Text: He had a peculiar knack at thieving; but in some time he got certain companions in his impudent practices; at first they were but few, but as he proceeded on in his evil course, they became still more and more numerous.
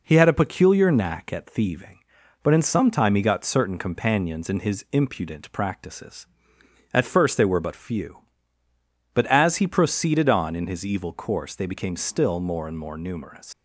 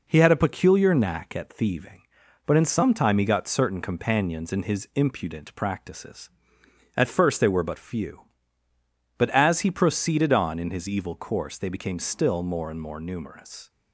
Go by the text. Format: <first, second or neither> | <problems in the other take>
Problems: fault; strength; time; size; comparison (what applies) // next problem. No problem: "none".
second | leaves "numerous" unfinished; at 13.5 s; 140 ms